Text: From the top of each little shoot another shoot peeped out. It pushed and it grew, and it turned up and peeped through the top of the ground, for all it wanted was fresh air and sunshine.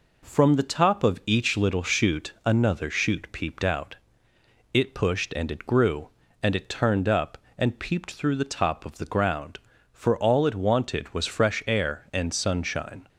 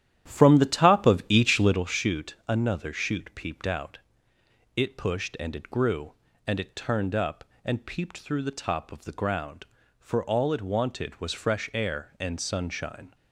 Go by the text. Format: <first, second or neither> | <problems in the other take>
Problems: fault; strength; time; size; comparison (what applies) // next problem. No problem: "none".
first | starts louder than the rest; strong; until 1.9 s; 11.5 dB